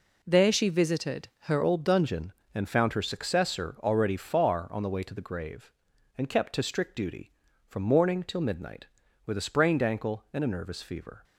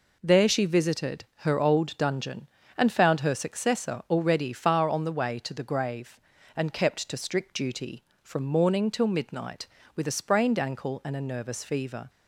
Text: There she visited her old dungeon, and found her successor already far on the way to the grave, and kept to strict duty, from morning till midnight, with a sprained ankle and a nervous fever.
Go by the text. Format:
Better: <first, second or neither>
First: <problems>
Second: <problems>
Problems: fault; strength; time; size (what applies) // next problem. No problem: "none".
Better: second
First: pauses between "visited" and "her"; slight; at 1.2 s; 0.18 s long // changes voice at "old"; from 1.6 s on; 9.6 s long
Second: pauses between "visited" and "her"; slight; at 1.2 s; 0.18 s long